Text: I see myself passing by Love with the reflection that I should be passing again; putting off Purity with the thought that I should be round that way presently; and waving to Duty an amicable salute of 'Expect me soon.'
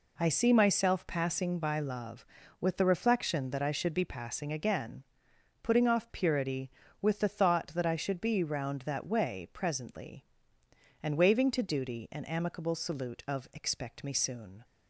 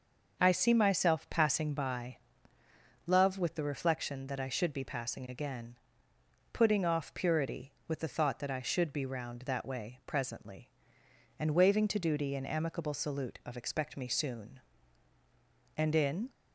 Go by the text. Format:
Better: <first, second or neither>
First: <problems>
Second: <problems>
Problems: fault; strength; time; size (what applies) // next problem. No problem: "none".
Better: first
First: none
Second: starts louder than the rest; until 1.4 s; 6.5 dB // pauses between "by" and "Love"; noticeable; at 2.1 s; 0.90 s long // goes on to say "And in"; from 15.7 s on; 0.54 s long